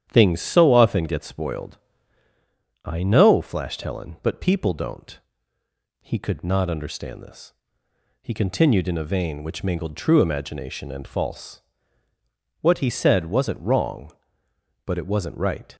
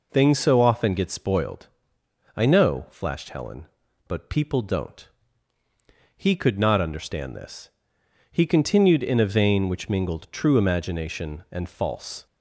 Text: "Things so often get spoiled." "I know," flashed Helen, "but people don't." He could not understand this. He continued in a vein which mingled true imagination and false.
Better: second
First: starts louder than the rest; strong; until 1.1 s; 9.5 dB // goes on to say "What he said wasn't wrong but it wasn't right"; strong; from 12.6 s on; 3.1 s long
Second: none

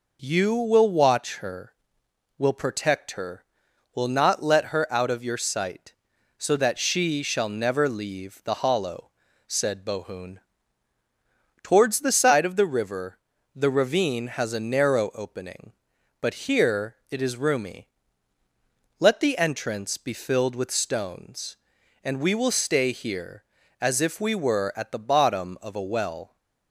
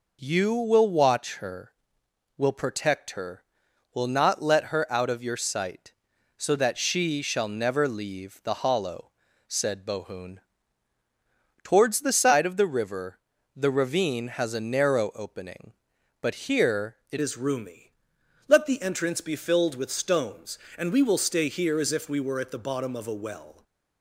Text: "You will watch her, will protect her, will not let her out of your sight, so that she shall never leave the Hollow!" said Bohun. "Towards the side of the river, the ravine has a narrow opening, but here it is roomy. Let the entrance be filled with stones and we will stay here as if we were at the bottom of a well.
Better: first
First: none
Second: changes voice at "is"; from 17.2 s on; 6.4 s long

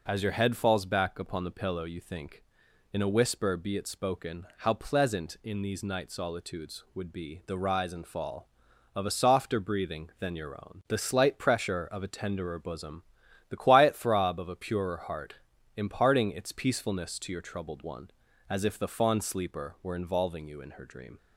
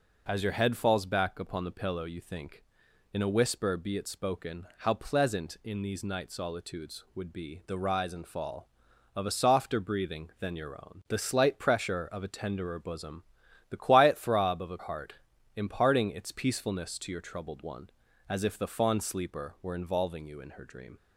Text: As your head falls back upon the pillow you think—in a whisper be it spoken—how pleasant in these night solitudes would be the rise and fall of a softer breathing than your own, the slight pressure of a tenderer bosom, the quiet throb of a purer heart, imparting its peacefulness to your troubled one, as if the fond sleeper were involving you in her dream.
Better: first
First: none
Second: skips "purer"; at 14.7 s

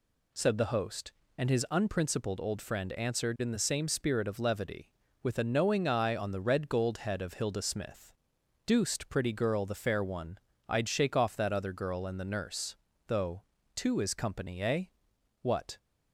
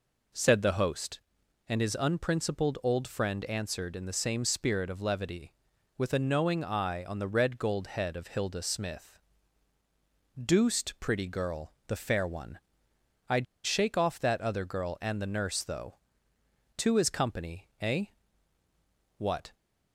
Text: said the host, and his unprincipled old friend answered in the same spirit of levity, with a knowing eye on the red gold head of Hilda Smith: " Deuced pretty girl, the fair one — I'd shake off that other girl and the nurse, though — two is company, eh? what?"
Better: first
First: none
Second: pauses between "I'd" and "shake"; slight; at 13.4 s; 0.20 s long

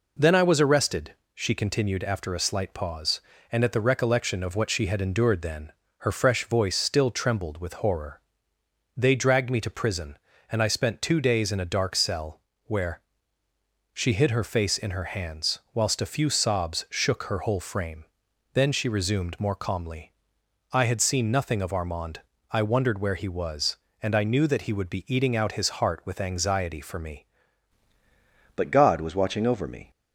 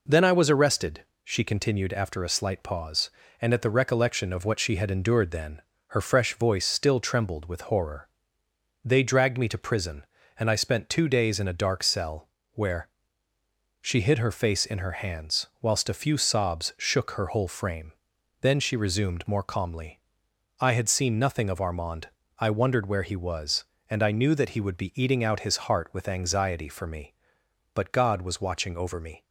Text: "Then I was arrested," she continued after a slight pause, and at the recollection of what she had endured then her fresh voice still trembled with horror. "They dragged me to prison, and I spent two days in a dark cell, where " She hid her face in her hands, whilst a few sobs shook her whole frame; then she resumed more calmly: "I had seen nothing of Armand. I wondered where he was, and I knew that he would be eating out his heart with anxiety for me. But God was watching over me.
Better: second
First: pauses between "then" and "her"; slight; at 5.7 s; 0.30 s long // changes voice at "But"; from 28.5 s on; 1.4 s long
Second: pauses between "then" and "her"; slight; at 5.6 s; 0.30 s long

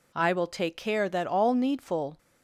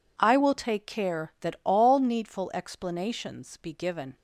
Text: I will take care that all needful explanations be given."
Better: second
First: stops before "explanations be given"; at 2.1 s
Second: none

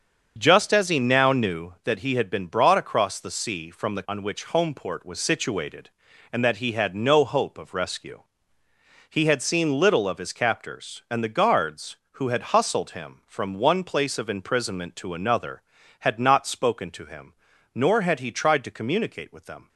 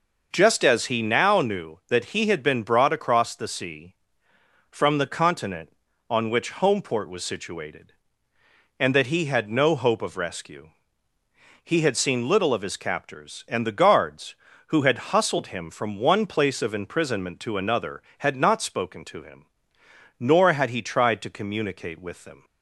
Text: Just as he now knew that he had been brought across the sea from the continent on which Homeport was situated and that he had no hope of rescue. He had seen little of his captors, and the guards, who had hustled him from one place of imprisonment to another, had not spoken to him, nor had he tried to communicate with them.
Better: second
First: starts louder than the rest; strong; until 1.3 s; 7 dB // skips "continent"; at 4.0 s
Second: none

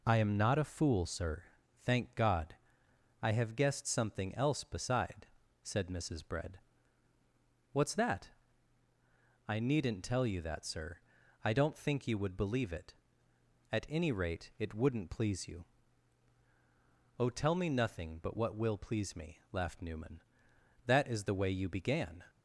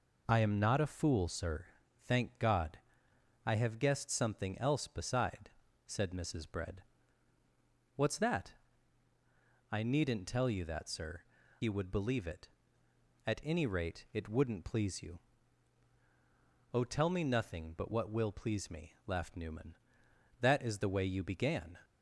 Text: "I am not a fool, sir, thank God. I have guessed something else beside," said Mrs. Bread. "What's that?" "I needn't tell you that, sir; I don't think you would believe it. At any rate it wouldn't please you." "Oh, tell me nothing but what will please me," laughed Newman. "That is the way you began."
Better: first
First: none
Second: skips "I don't think"; at 11.4 s

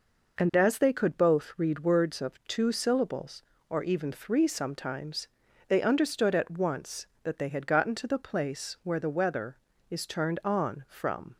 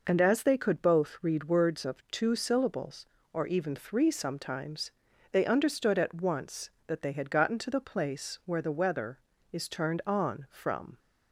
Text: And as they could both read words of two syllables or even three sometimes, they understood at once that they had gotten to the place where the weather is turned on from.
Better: neither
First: none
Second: none

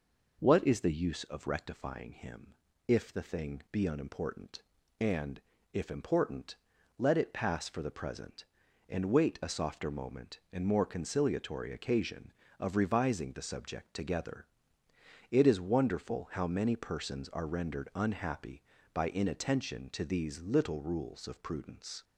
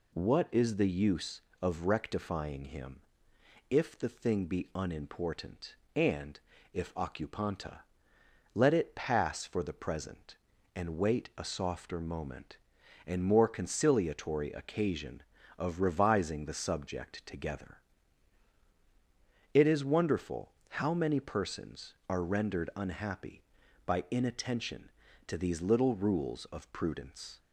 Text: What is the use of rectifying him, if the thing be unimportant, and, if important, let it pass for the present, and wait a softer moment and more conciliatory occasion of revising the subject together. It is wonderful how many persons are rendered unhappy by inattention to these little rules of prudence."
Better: first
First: none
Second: says "occupanta" for "important"; at 6.9 s // pauses between "wonderful" and "how"; slight; at 20.5 s; 0.16 s long

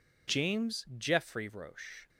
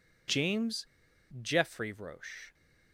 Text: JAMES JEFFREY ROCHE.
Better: first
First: none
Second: pauses between "JAMES" and "JEFFREY"; noticeable; at 0.8 s; 0.56 s long

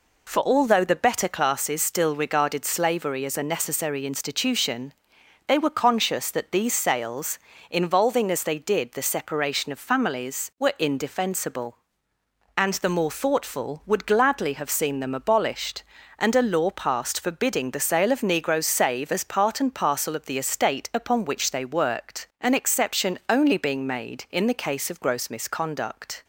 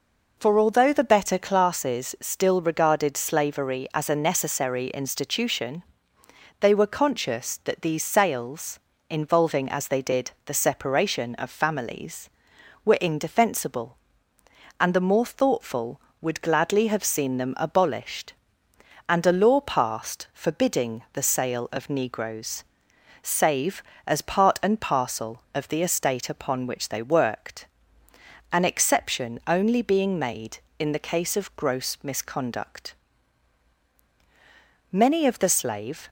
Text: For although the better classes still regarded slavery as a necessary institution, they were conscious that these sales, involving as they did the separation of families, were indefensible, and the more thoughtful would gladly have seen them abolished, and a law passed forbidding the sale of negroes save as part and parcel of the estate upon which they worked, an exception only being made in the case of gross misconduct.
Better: first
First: none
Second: pauses between "negroes" and "save"; noticeable; at 22.6 s; 0.58 s long // goes on to say "Many of the slave"; noticeable; from 34.9 s on; 1.1 s long

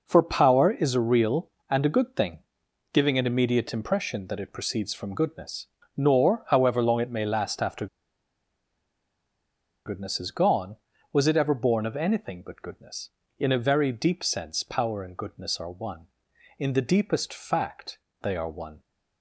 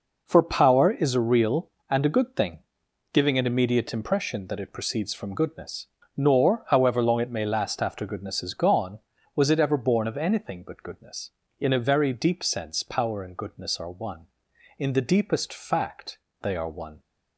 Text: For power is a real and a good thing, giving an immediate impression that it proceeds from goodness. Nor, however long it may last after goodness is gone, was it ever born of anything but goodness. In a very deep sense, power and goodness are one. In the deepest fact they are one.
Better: second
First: pauses between "after" and "goodness"; strong; at 7.8 s; 1.9 s long // pauses between "fact" and "they"; slight; at 17.9 s; 0.24 s long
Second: pauses between "fact" and "they"; slight; at 16.1 s; 0.24 s long

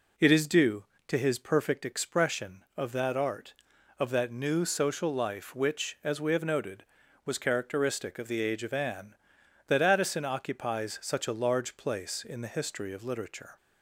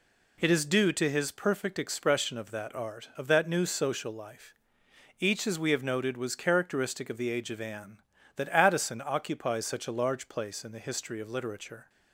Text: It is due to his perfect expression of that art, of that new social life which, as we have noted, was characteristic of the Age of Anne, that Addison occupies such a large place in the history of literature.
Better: first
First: none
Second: says "each" for "which"; at 5.2 s

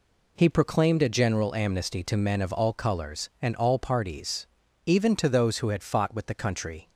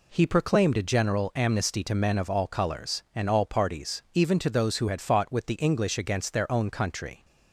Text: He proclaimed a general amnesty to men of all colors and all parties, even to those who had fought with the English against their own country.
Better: second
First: skips "English against their own"; at 6.3 s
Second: none

